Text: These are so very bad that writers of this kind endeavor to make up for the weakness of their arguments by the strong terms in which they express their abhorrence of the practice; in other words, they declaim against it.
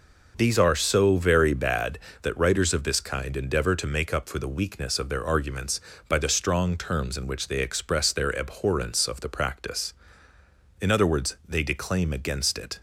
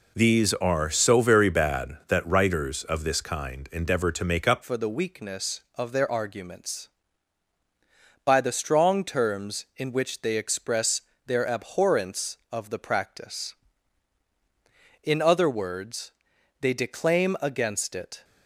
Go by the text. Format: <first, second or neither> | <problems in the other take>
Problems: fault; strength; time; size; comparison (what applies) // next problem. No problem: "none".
first | changes voice at "for"; from 4.6 s on; 13.6 s long // pauses between "express" and "their"; slight; at 11.0 s; 0.24 s long